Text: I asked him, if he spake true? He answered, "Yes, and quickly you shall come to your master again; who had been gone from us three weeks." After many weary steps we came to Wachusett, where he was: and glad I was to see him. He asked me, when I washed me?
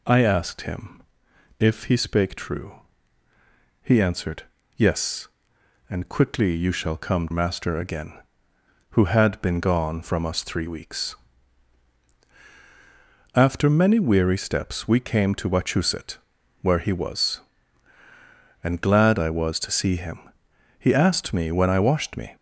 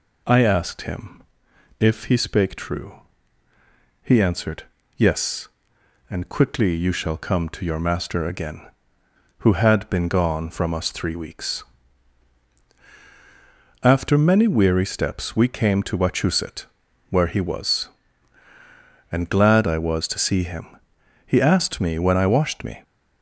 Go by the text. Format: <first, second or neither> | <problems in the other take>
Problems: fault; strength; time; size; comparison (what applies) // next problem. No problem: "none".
second | skips "to your"; at 7.3 s